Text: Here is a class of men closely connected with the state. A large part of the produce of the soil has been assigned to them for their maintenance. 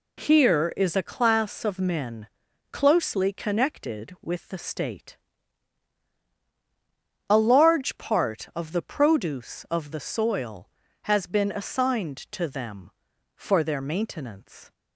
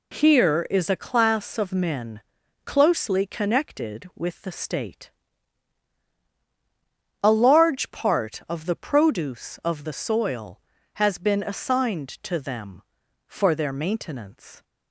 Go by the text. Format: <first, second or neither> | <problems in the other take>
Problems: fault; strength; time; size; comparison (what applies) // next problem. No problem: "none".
neither | pauses between "men" and "closely"; noticeable; the same in both